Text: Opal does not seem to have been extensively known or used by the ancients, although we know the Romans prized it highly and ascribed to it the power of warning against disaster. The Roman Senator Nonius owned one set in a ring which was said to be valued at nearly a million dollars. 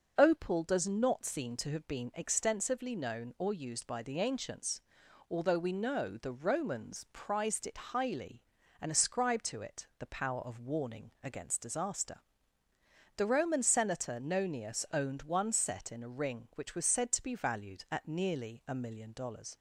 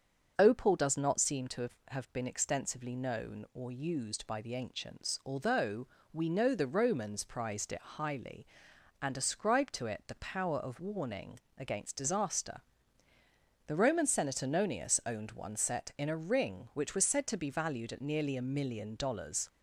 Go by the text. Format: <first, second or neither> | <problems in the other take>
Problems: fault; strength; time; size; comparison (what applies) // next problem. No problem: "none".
first | starts louder than the rest; strong; until 1.3 s; 7 dB; noticeable in the first // says "have" twice; at 1.8 s // pauses between "although" and "we"; slight; at 5.8 s; 0.24 s long // pauses between "warning" and "against"; slight; at 11.3 s; 0.18 s long